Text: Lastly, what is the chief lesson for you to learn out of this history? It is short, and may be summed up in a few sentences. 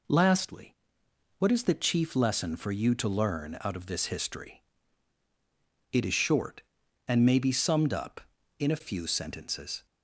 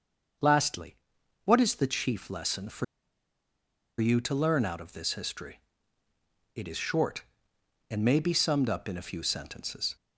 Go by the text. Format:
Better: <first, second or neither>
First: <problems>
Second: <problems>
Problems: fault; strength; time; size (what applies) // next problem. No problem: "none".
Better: first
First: none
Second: starts louder than the rest; until 1.9 s; 6.5 dB // pauses between "for" and "you"; at 2.8 s; 1.1 s long